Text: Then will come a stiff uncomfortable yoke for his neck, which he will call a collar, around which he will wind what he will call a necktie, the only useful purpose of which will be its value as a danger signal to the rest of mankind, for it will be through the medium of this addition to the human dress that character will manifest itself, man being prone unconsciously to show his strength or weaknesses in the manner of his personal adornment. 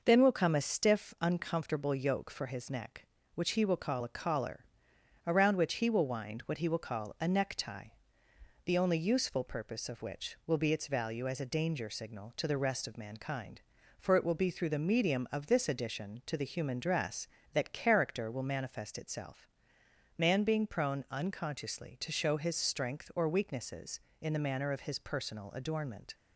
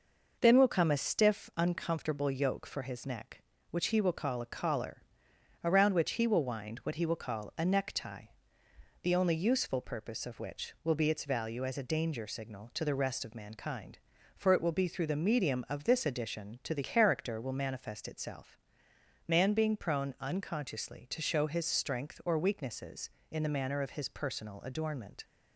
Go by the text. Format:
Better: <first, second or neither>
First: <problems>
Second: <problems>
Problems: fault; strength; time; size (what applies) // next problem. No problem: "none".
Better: first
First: none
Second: skips "human dress that"; at 16.8 s